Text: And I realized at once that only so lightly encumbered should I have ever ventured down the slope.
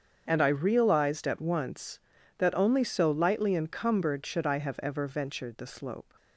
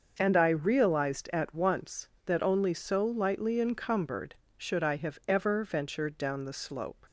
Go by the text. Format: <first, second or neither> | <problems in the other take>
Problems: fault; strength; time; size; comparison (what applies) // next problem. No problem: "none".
second | starts louder than the rest; strong; until 1.2 s; 7.5 dB; also in the second // skips "down"; at 5.5 s